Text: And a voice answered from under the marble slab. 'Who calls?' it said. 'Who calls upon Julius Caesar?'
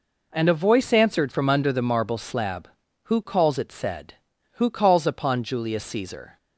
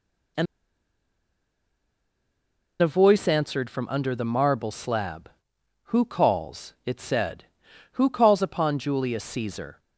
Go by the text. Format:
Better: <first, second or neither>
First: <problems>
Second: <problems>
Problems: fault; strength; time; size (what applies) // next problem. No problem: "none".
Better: first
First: none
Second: pauses between "And" and "a"; strong; at 0.4 s; 2.3 s long